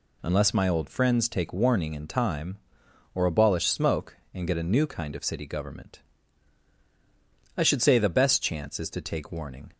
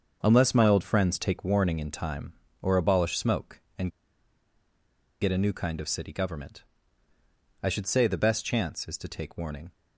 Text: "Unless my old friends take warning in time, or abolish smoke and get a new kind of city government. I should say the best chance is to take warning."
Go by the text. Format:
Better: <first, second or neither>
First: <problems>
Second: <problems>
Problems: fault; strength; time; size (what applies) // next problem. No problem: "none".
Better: first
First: none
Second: starts louder than the rest; until 1.2 s; 6.5 dB // pauses between "and" and "get"; strong; at 3.8 s; 1.3 s long